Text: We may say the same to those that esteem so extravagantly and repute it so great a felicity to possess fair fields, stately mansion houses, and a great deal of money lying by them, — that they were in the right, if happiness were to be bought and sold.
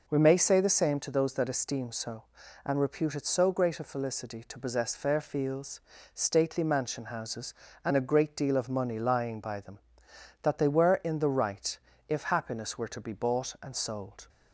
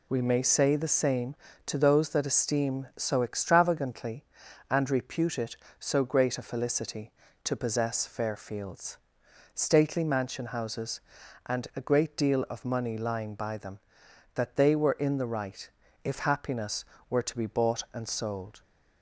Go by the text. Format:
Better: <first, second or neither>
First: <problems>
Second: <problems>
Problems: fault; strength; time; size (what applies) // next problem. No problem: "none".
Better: second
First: skips "extravagantly"; at 2.4 s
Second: none